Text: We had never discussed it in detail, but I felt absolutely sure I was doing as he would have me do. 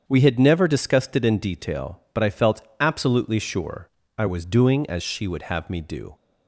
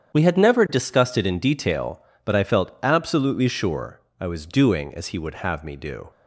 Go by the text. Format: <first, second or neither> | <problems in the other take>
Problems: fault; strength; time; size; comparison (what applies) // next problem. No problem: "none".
second | starts louder than the rest; strong; until 1.0 s; 7.5 dB; strong in the second // pauses between "felt" and "absolutely"; slight; at 2.6 s; 0.18 s long // pauses between "sure" and "I"; slight; at 3.8 s; 0.30 s long; slight in the second // says "she" for "he"; at 5.0 s